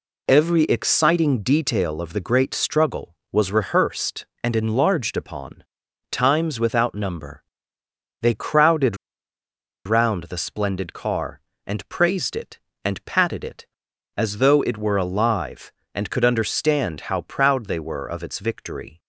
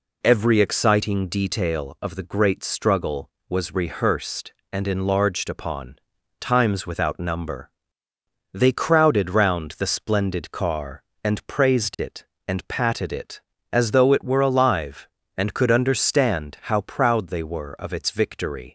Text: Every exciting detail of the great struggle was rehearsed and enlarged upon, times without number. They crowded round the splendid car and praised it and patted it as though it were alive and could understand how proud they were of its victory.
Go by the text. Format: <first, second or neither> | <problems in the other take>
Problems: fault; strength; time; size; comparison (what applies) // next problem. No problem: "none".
second | pauses between "crowded" and "round"; noticeable; at 8.9 s; 0.89 s long